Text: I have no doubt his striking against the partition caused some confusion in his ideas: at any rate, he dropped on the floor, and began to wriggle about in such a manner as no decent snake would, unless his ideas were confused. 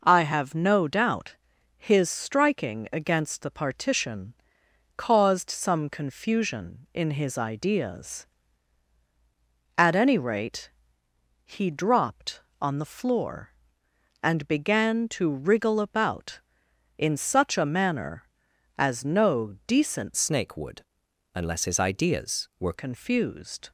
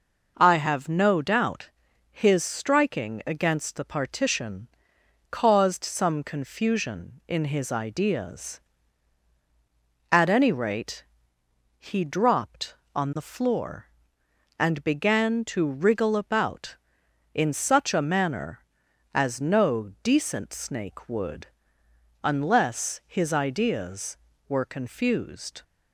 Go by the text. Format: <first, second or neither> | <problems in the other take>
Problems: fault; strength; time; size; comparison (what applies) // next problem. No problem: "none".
second | pauses between "doubt" and "his"; at 1.3 s; 0.42 s long; also in the second // pauses between "partition" and "caused"; noticeable; at 4.3 s; 0.62 s long; noticeable in the second // changes voice from "snake" to "were"; from 20.1 to 22.7 s; 2.6 s long